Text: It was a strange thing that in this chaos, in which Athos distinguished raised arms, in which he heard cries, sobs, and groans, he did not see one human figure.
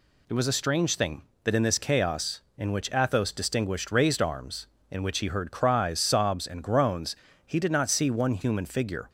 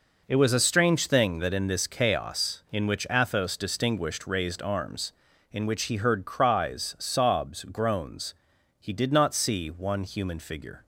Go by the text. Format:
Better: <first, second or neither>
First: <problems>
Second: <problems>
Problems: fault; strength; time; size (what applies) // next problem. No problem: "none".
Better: first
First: none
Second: skips "and"; at 7.6 s